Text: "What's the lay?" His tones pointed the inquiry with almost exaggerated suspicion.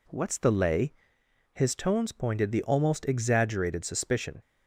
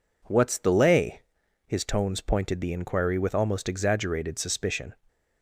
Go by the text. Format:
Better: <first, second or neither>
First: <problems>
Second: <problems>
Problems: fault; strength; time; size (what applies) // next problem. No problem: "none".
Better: second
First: skips "inquiry with"; at 2.6 s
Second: none